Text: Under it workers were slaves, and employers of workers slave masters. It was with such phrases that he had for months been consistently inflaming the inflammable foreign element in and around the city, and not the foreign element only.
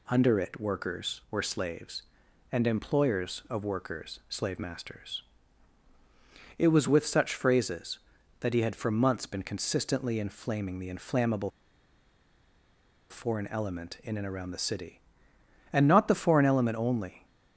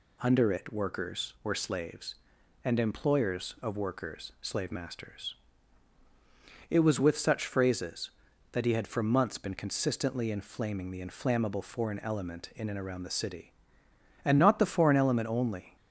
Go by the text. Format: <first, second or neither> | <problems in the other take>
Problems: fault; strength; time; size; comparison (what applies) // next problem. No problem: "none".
second | pauses between "inflammable" and "foreign"; strong; at 11.4 s; 1.6 s long